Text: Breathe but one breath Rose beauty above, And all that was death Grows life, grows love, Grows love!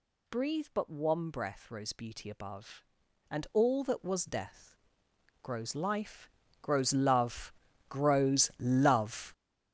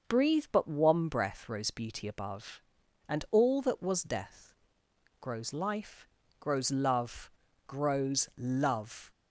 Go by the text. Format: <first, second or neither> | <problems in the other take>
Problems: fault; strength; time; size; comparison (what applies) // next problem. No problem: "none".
second | gets louder; strong; throughout; 10 dB // pauses between "death" and "Grows"; noticeable; at 4.7 s; 0.68 s long; noticeable in the second